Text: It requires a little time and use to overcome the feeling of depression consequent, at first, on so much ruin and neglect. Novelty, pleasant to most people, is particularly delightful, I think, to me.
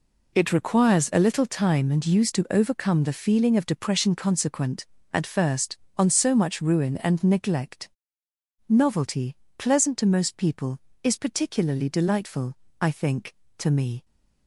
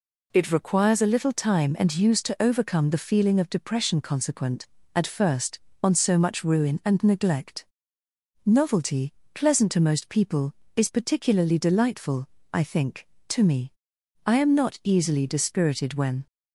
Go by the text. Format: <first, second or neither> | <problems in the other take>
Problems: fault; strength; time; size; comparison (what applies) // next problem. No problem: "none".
first | goes on to say "I am not easily dispirited when"; strong; from 14.2 s on; 2.0 s long